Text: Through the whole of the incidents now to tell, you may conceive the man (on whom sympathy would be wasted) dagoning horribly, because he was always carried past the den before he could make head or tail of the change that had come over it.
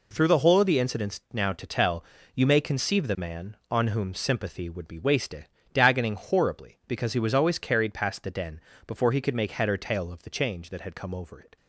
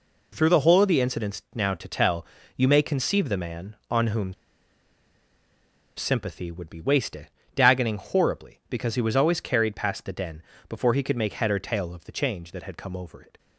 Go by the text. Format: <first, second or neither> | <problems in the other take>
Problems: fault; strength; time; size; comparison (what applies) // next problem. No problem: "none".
first | pauses between "whom" and "sympathy"; strong; at 4.3 s; 1.6 s long // pauses between "den" and "before"; slight; at 10.4 s; 0.26 s long; slight in the first